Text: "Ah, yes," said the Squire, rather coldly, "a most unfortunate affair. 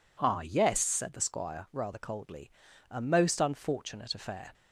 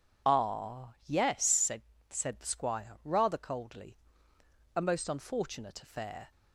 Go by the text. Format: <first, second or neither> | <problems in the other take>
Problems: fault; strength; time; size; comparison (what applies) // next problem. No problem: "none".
first | says "said" twice; at 2.0 s